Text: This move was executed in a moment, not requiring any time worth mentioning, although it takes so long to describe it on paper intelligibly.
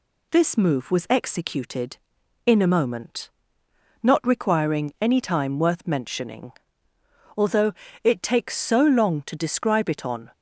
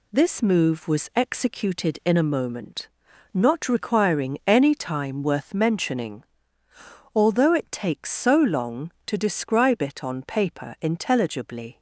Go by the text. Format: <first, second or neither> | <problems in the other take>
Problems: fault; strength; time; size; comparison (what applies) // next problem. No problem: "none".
second | pauses between "although" and "it"; slight; at 7.7 s; 0.30 s long // stops before "paper intelligibly"; at 10.3 s